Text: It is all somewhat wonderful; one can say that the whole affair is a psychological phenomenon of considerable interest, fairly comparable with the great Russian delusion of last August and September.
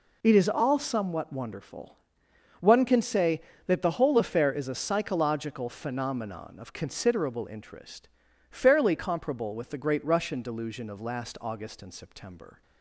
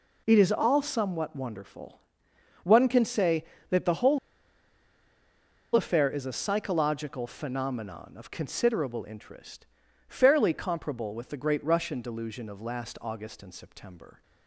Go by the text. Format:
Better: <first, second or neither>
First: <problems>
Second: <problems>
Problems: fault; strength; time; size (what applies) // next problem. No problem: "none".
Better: first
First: none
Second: pauses between "whole" and "affair"; strong; at 4.1 s; 1.5 s long